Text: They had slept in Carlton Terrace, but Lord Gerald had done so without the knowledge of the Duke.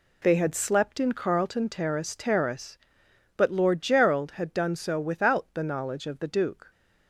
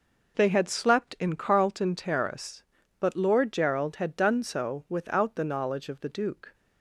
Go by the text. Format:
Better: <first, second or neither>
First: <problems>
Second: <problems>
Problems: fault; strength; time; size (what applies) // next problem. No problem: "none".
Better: second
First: says "Terrace" twice; at 2.1 s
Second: none